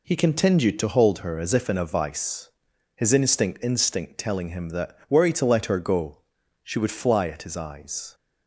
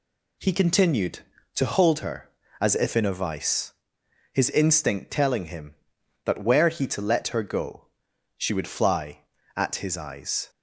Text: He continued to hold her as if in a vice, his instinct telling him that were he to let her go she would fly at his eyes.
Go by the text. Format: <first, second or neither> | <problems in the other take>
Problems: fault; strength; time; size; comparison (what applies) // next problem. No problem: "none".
second | says "instinct" twice; at 3.6 s // pauses between "go" and "she"; at 6.1 s; 0.44 s long; noticeable in the second